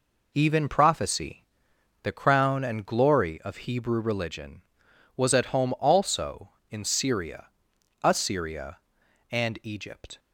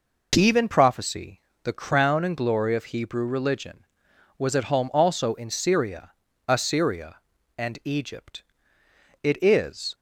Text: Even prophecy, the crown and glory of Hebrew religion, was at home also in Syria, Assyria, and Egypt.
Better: first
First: none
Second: goes on to say "It is"; noticeable; from 9.2 s on; 0.72 s long

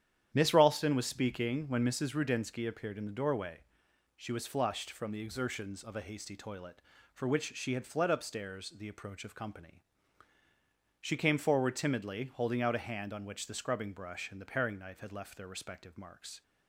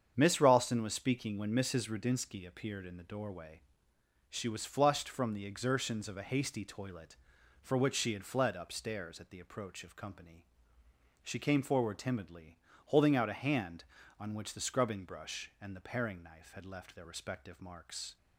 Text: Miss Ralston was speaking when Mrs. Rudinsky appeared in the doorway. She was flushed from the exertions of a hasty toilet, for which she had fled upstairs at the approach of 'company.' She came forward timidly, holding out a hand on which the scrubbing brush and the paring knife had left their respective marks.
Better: second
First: starts louder than the rest; strong; until 1.3 s; 10 dB // skips "at"; at 8.6 s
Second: starts louder than the rest; strong; until 1.1 s; 8 dB

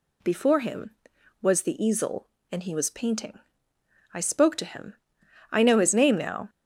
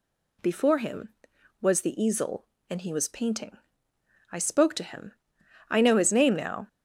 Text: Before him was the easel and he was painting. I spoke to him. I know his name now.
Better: neither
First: none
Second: none

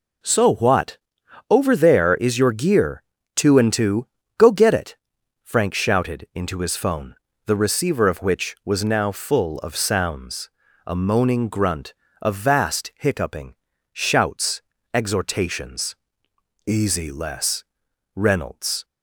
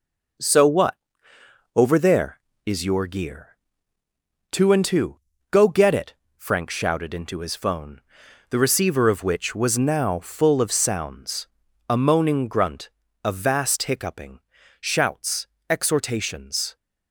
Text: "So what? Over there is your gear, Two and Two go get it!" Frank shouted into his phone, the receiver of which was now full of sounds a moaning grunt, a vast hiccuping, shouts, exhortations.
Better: second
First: pauses between "Two" and "go"; slight; at 4.0 s; 0.32 s long // pauses between "sounds" and "a"; at 10.4 s; 0.38 s long // goes on to say "Easy Les Reynolds"; strong; from 16.6 s on; 2.1 s long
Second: pauses between "Two" and "go"; slight; at 5.1 s; 0.32 s long // pauses between "sounds" and "a"; at 11.4 s; 0.42 s long

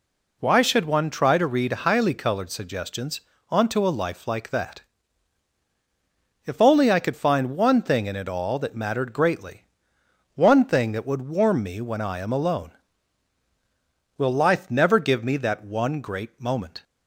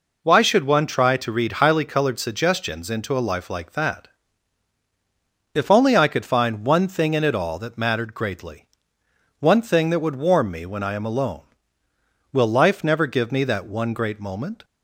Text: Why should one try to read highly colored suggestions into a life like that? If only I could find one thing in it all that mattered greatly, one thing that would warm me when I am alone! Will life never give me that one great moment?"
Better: second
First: says "onto" for "into"; at 3.4 s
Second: none

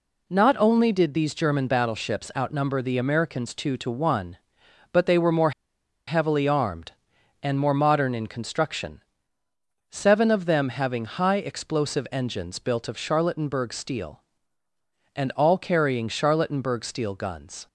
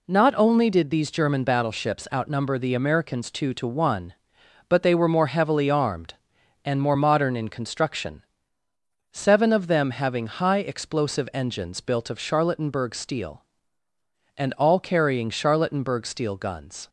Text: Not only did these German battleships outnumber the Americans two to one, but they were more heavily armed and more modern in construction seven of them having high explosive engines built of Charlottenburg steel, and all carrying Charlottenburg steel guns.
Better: second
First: pauses between "more" and "heavily"; noticeable; at 5.5 s; 0.56 s long // pauses between "construction" and "seven"; noticeable; at 9.0 s; 0.90 s long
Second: pauses between "construction" and "seven"; noticeable; at 8.2 s; 0.90 s long

